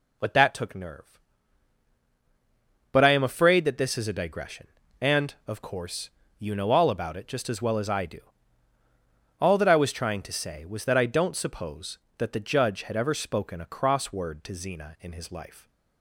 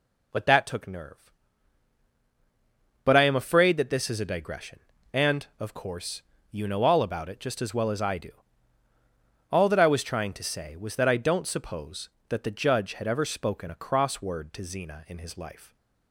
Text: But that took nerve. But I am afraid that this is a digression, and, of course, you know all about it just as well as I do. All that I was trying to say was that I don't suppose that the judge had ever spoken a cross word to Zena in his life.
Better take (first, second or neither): neither